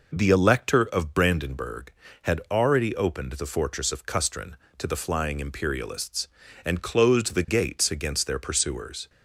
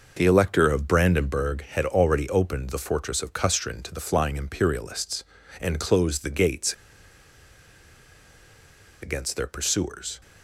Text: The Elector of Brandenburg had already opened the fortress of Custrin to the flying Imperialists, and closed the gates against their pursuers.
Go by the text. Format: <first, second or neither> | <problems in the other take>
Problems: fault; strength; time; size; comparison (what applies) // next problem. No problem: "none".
first | pauses between "gates" and "against"; strong; at 6.7 s; 2.2 s long